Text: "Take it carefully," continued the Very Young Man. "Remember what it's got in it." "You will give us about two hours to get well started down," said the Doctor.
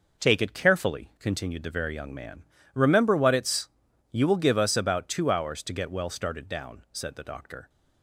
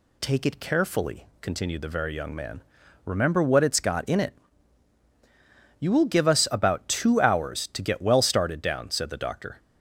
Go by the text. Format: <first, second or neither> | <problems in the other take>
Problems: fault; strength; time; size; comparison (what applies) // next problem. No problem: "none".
second | skips "got in it"; at 3.8 s